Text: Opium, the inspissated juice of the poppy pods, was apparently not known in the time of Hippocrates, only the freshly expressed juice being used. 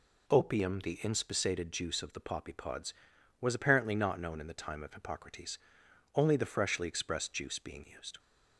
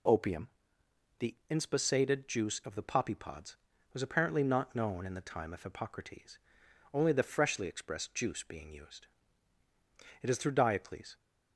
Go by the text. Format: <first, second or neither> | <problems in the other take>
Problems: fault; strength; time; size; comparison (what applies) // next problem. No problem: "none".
first | pauses between "the" and "inspissated"; slight; at 1.3 s; 0.16 s long // goes on to say "It is through Diocles"; noticeable; from 10.2 s on; 0.94 s long